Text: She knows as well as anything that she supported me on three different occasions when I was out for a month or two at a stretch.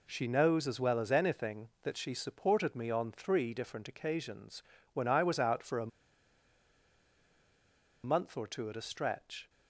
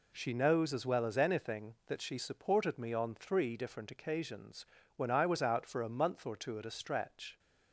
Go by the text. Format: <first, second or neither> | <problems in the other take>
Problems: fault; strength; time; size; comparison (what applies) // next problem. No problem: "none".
second | pauses between "occasions" and "when"; slight; at 4.6 s; 0.32 s long; slight in the second // pauses between "a" and "month"; strong; at 5.9 s; 2.1 s long